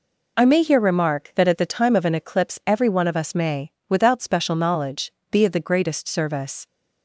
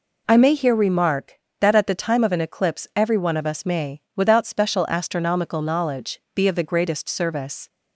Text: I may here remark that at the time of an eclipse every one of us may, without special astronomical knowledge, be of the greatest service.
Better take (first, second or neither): second